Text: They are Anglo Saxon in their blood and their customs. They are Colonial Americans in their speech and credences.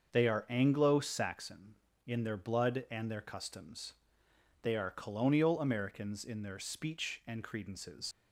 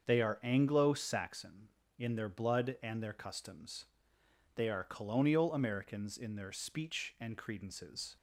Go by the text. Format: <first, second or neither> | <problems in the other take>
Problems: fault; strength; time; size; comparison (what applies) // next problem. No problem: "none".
second | starts louder than the rest; until 1.1 s; 6.5 dB; also in the second // leaves "credences" unfinished; at 8.1 s; 105 ms